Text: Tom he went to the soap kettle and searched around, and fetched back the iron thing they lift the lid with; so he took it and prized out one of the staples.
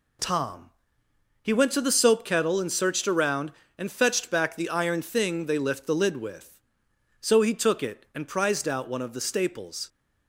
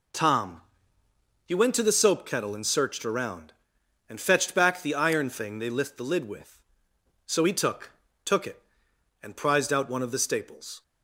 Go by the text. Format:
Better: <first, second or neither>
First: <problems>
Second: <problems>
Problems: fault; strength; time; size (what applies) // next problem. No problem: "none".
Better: first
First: pauses between "Tom" and "he"; noticeable; at 0.6 s; 0.76 s long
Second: pauses between "Tom" and "he"; noticeable; at 0.6 s; 0.84 s long // says "took" twice; at 8.2 s